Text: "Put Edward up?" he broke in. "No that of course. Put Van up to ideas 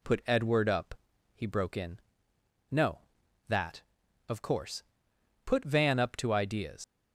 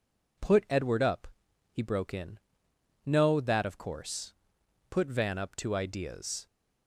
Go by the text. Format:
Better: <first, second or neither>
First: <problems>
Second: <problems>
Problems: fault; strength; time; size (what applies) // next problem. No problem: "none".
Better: second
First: leaves "ideas" unfinished; at 6.8 s; 115 ms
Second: none